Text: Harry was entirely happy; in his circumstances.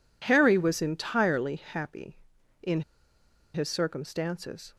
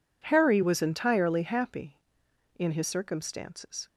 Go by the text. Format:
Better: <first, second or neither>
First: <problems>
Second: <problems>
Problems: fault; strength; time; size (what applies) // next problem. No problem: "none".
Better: second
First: pauses between "in" and "his"; noticeable; at 2.8 s; 0.71 s long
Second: none